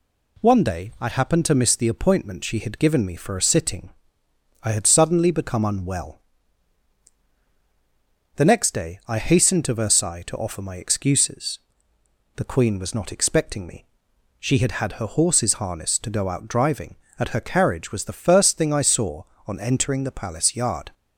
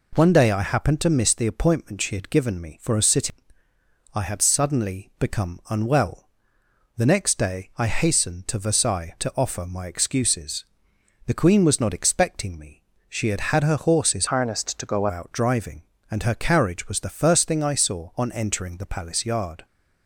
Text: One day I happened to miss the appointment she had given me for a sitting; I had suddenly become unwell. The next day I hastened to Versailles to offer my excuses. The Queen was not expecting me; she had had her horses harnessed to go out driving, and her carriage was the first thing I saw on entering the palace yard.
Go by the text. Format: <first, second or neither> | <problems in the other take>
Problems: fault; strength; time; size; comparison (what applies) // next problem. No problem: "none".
first | changes voice from "harnessed" to "go"; from 14.2 to 15.0 s; 0.8 s long